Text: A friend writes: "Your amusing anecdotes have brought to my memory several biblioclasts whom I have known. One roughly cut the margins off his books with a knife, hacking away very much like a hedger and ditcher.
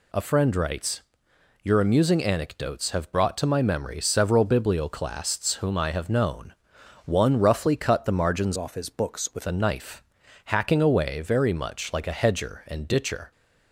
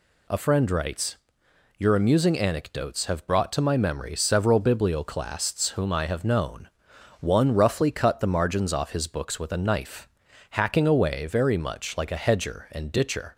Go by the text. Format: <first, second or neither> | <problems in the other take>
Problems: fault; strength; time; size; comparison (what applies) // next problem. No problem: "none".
second | changes voice from "off" to "with"; from 8.5 to 9.4 s; 0.9 s long